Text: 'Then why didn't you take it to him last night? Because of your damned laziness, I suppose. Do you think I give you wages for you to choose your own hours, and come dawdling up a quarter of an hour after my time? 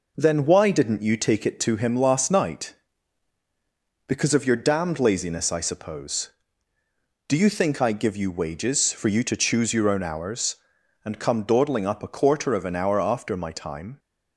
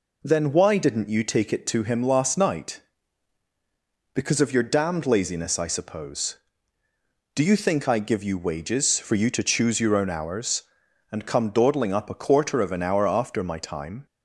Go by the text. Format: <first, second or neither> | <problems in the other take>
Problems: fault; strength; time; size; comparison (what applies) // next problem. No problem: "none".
second | gets quieter; throughout; 3.5 dB